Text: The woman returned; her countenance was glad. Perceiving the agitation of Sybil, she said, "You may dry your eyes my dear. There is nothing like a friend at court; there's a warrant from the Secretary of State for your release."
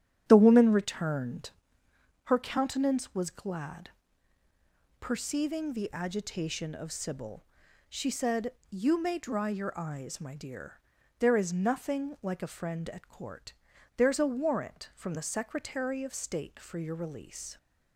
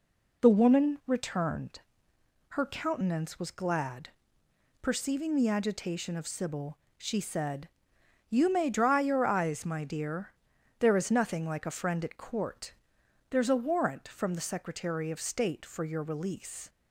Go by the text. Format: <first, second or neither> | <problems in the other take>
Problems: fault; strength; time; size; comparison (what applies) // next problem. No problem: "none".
second | starts louder than the rest; strong; until 2.0 s; 11 dB